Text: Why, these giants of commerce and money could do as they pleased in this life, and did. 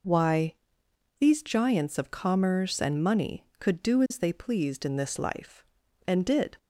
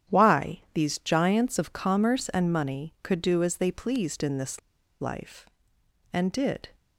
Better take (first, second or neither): first